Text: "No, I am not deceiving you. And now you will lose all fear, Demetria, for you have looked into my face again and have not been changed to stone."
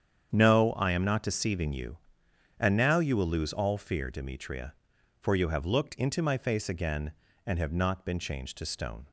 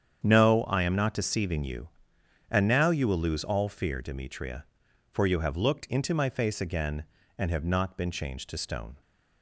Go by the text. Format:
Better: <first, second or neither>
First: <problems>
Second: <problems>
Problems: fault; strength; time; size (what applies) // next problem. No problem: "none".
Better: neither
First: starts louder than the rest; strong; until 1.3 s; 8 dB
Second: starts louder than the rest; strong; until 1.2 s; 8 dB